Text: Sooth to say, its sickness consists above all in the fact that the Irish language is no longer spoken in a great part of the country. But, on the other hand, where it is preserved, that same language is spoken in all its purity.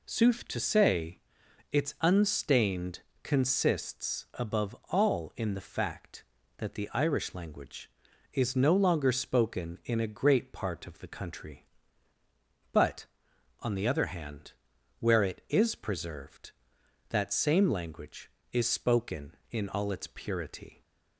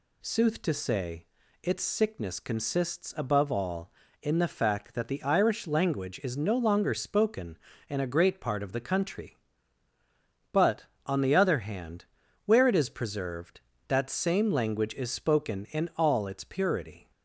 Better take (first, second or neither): second